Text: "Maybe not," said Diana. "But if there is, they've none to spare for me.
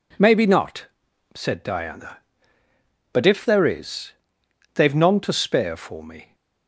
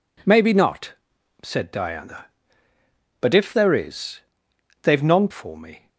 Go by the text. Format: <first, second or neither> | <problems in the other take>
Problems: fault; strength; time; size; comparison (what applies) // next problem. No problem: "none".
first | skips "to spare"; at 5.2 s